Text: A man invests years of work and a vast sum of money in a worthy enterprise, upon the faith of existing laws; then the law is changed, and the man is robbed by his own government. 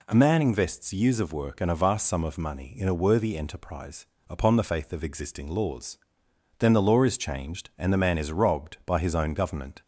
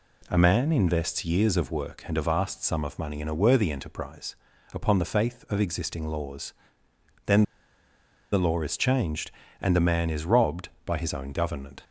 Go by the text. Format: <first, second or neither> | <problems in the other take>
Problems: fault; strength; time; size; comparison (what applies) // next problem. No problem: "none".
first | pauses between "then" and "the"; noticeable; at 7.4 s; 0.89 s long